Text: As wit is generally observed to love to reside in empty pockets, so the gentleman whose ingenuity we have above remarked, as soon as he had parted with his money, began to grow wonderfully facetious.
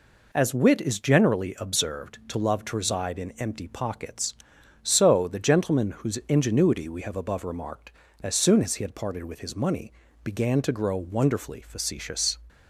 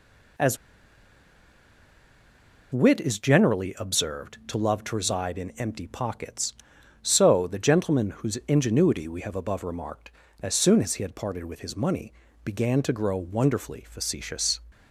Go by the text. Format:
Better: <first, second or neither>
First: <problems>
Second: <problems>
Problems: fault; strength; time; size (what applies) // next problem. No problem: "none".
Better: first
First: none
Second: pauses between "As" and "wit"; strong; at 0.5 s; 2.1 s long